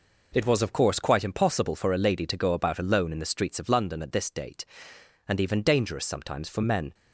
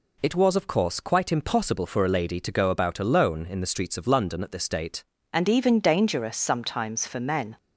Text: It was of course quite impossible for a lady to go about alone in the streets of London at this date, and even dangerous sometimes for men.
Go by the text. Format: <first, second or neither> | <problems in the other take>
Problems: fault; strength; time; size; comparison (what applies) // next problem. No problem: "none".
first | changes voice at "and"; from 5.3 s on; 2.2 s long